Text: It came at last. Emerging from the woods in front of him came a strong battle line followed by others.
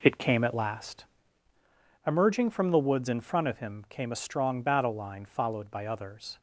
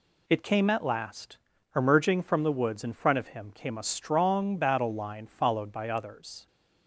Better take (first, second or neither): second